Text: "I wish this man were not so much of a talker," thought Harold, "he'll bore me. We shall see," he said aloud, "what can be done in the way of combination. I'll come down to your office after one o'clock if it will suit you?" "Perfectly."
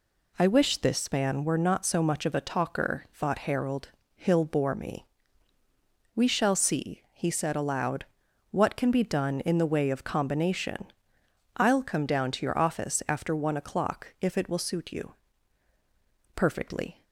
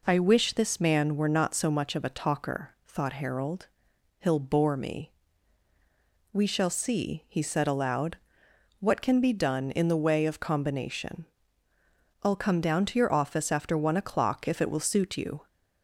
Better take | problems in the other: first | stops before "Perfectly"; at 15.4 s

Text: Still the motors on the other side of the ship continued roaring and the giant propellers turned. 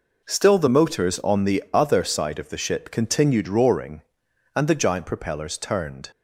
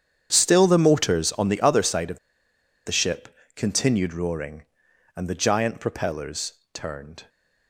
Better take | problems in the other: first | starts louder than the rest; strong; until 1.3 s; 8.5 dB // pauses between "of" and "the"; noticeable; at 2.1 s; 0.68 s long // pauses between "ship" and "continued"; slight; at 3.2 s; 0.26 s long // pauses between "propellers" and "turned"; slight; at 6.5 s; 0.18 s long

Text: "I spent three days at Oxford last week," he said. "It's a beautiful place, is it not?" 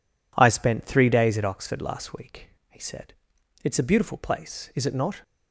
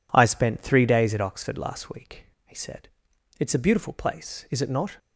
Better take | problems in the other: neither | none

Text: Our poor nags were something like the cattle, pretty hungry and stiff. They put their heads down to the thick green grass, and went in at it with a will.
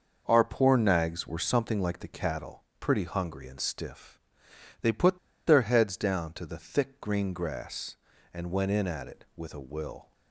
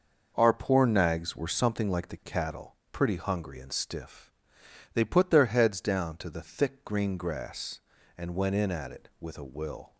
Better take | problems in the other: second | pauses between "put" and "their"; slight; at 5.1 s; 0.28 s long

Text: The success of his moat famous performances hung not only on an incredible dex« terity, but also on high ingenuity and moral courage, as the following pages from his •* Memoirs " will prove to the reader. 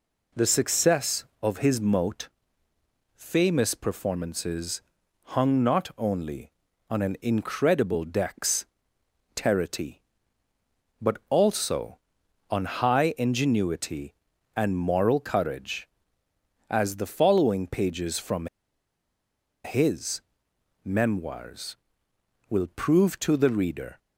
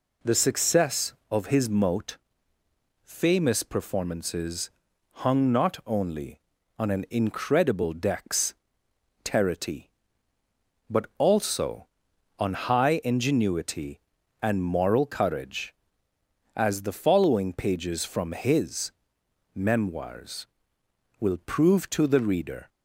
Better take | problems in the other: second | pauses between "moat" and "famous"; noticeable; at 2.2 s; 0.86 s long; noticeable in the second // pauses between "performances" and "hung"; noticeable; at 4.8 s; 0.56 s long; noticeable in the second // pauses between "dex" and "terity"; noticeable; at 8.6 s; 0.72 s long; noticeable in the second // pauses between "from" and "his"; at 18.4 s; 1.1 s long

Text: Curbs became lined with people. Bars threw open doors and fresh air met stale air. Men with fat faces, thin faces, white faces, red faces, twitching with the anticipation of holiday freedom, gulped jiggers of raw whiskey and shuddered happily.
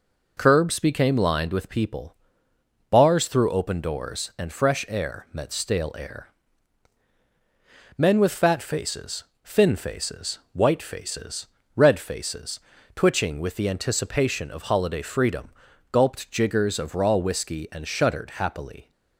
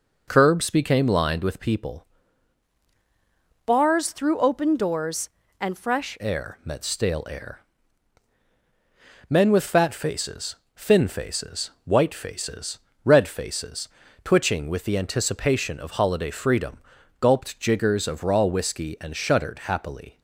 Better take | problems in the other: first | changes voice from "Bars" to "fresh"; from 3.6 to 6.1 s; 2.5 s long

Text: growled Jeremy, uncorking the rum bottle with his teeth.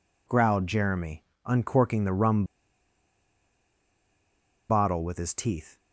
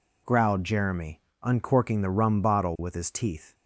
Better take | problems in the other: second | pauses between "rum" and "bottle"; strong; at 2.4 s; 2.2 s long

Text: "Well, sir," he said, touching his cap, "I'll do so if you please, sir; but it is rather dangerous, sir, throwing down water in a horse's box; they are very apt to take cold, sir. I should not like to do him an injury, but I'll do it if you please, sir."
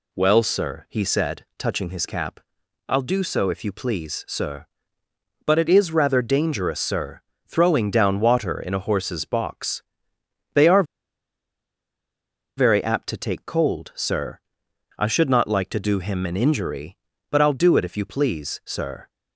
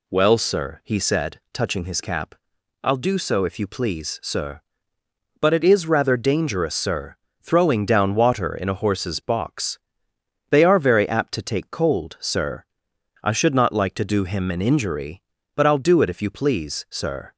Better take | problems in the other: second | pauses between "are" and "very"; strong; at 10.8 s; 1.7 s long

